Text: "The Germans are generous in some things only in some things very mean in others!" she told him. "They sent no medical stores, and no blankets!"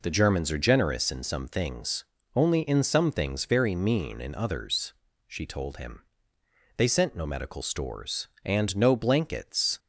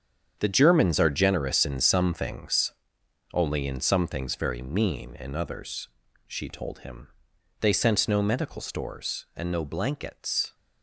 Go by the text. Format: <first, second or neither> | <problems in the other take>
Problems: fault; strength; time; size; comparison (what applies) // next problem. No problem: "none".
first | gets quieter; strong; throughout; 11 dB // pauses between "things" and "only"; noticeable; at 2.7 s; 0.60 s long; slight in the first